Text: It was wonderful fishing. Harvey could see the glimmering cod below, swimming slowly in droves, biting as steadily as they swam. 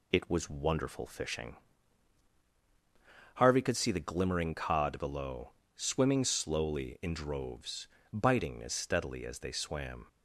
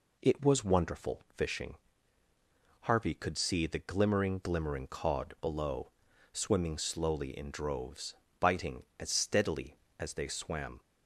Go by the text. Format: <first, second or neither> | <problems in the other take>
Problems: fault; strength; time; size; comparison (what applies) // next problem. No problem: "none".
first | says "glimmering" twice; at 4.3 s